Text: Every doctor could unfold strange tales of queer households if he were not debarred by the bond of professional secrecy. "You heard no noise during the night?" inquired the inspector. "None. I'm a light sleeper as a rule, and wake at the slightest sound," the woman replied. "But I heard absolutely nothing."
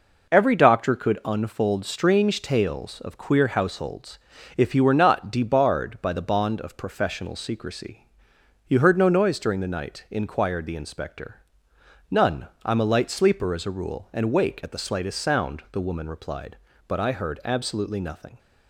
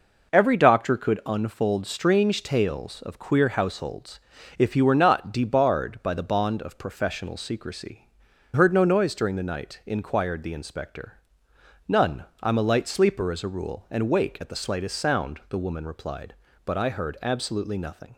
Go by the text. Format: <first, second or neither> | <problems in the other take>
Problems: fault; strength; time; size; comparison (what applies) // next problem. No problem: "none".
first | pauses between "households" and "if"; at 4.1 s; 0.40 s long; also in the first // skips "You"; at 8.3 s